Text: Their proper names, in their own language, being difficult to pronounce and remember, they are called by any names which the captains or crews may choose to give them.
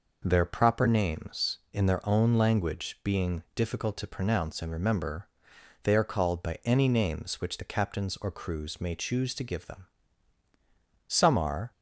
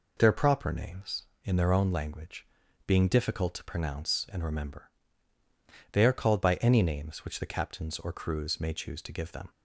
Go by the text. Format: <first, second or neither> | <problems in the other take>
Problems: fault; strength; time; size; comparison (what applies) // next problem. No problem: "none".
second | goes on to say "Some are"; noticeable; from 11.0 s on; 0.62 s long